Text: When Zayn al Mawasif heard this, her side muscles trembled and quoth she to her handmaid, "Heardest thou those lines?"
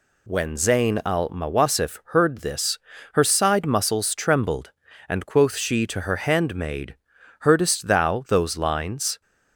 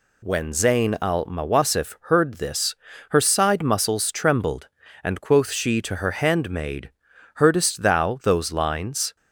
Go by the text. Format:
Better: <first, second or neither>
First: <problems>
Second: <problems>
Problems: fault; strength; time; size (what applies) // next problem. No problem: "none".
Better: neither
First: none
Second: none